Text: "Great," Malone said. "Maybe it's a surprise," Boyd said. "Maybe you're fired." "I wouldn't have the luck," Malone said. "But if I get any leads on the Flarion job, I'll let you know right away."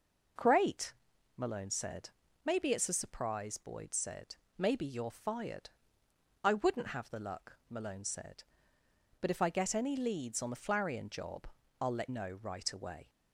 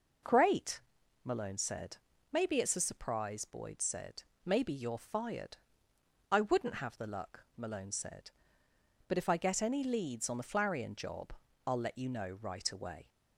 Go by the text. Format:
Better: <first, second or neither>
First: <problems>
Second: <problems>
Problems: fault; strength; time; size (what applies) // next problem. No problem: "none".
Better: second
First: skips "you"; at 12.0 s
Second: none